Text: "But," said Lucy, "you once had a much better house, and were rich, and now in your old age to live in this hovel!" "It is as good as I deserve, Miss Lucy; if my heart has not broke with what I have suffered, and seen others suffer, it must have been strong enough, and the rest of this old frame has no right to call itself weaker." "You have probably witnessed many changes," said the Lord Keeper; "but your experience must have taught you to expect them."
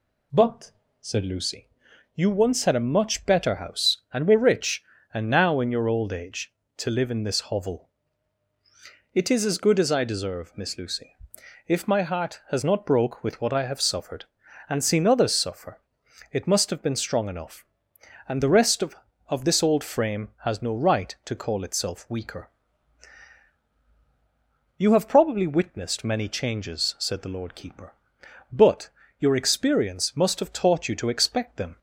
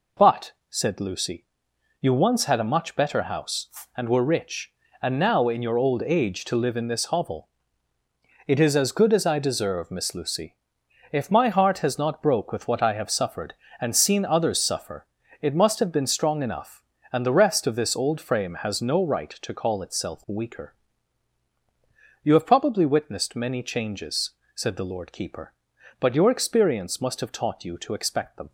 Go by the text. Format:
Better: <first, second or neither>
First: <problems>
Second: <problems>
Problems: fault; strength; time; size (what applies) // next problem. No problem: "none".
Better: second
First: says "of" twice; at 19.2 s // pauses between "but" and "your"; slight; at 28.8 s; 0.30 s long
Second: none